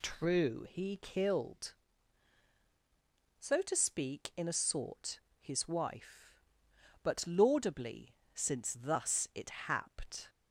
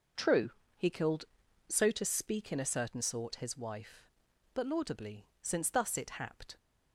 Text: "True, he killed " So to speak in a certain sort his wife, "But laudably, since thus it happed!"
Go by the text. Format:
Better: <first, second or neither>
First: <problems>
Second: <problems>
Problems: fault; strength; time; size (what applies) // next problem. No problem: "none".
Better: second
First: skips "certain"; at 4.5 s // pauses between "sort" and "his"; slight; at 5.1 s; 0.20 s long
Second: none